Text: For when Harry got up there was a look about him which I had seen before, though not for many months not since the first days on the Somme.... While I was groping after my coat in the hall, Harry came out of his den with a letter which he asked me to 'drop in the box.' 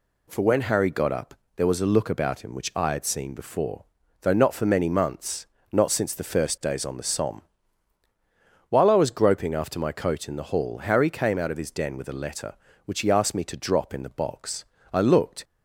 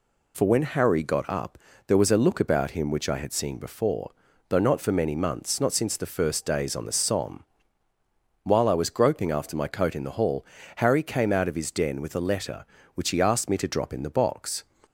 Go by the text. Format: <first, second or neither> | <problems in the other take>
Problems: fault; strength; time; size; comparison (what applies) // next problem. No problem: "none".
second | pauses between "up" and "there"; slight; at 1.3 s; 0.22 s long; slight in the second // pauses between "months" and "not"; slight; at 5.4 s; 0.26 s long // goes on to say "I looked"; from 14.9 s on; 0.50 s long